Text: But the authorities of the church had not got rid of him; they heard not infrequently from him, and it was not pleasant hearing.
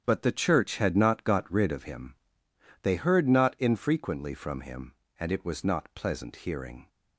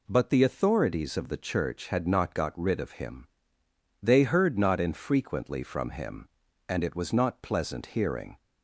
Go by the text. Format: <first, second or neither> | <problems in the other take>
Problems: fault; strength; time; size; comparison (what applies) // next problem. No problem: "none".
second | starts louder than the rest; strong; until 1.0 s; 8.5 dB // skips "the authorities of"; at 0.2 s